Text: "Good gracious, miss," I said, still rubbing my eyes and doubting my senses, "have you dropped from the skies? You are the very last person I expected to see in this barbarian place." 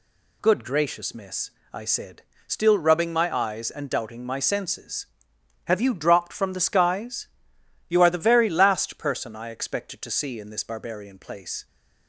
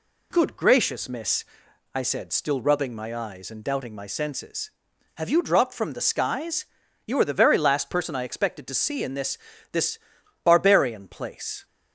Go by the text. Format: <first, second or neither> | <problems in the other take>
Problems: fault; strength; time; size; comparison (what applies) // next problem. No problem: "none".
first | says "this" twice; at 9.7 s